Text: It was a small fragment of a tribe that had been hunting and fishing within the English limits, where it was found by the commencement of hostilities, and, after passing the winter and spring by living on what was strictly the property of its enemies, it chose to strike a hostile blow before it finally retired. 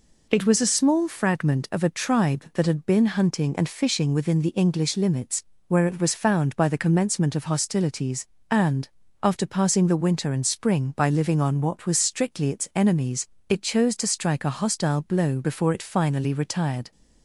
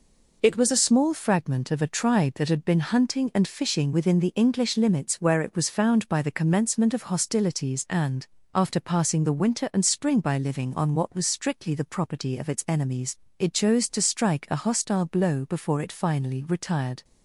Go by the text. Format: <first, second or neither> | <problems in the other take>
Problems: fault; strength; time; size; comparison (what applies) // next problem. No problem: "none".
second | skips "the property of"; at 12.5 s